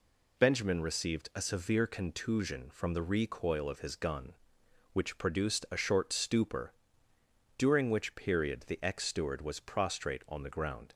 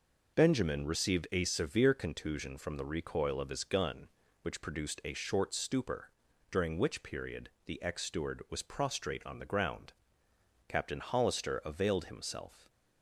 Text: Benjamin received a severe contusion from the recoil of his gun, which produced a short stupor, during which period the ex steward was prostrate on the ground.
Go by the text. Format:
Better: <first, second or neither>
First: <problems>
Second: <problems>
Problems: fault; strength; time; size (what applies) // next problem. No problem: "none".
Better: first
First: none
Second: pauses between "period" and "the"; slight; at 7.4 s; 0.16 s long // goes on to say "Captain Hollister availed himself"; strong; from 10.6 s on; 2.0 s long